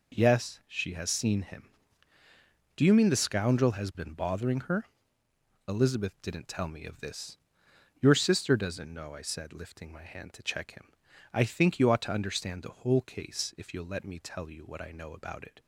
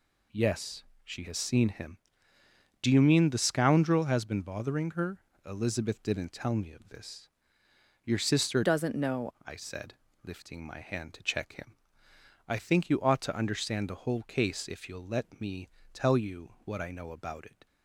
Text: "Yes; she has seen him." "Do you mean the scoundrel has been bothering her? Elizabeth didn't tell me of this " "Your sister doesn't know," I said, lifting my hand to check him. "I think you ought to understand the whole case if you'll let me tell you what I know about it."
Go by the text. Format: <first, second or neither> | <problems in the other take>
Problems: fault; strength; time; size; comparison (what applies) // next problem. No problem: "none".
first | changes voice from "doesn't" to "know"; from 8.6 to 9.2 s; 0.6 s long // pauses between "me" and "tell"; slight; at 15.6 s; 0.22 s long